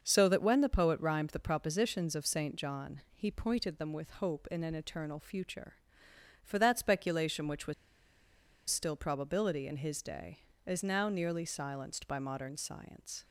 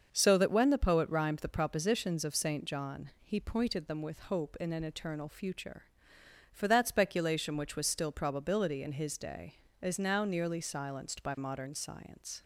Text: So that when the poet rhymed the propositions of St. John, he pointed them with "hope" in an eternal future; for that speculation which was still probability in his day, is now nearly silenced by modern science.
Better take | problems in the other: second | starts louder than the rest; until 1.0 s; 6.5 dB; also in the second // pauses between "was" and "still"; noticeable; at 7.7 s; 0.96 s long

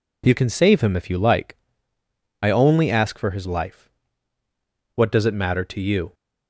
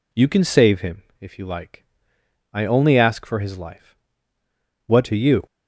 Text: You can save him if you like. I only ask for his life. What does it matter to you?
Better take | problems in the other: first | pauses between "him" and "if"; slight; at 1.0 s; 0.18 s long // skips "does it matter"; at 5.0 s

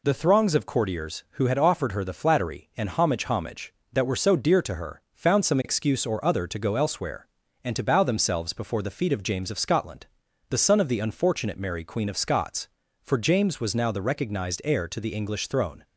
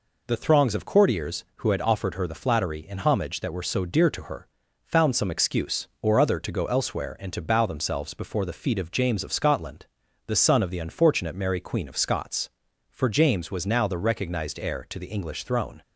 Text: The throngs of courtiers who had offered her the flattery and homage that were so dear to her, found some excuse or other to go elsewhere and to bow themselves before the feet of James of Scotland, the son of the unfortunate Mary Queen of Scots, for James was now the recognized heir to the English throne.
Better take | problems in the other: second | says "homage" twice; at 3.2 s

